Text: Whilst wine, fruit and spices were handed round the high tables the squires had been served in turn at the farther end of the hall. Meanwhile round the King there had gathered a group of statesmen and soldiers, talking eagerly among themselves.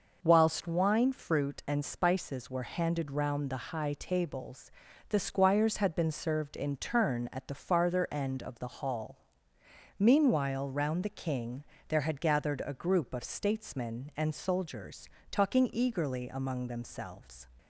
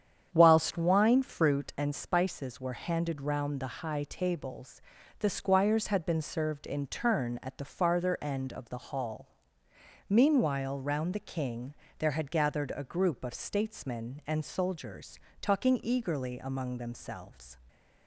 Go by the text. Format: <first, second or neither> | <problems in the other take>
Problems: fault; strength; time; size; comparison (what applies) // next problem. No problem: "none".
first | starts louder than the rest; strong; until 1.8 s; 8.5 dB // pauses between "tables" and "the"; at 4.8 s; 0.38 s long; also in the first // pauses between "King" and "there"; slight; at 11.7 s; 0.24 s long; slight in the first